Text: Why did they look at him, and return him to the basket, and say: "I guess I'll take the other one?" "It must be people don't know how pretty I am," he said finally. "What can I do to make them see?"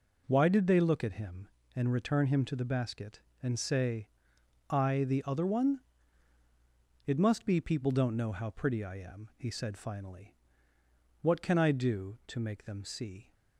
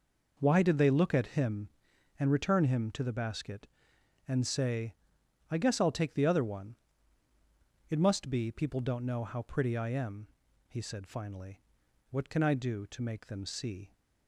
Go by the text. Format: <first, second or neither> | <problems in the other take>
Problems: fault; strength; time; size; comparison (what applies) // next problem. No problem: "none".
second | skips "guess I'll take"; at 5.0 s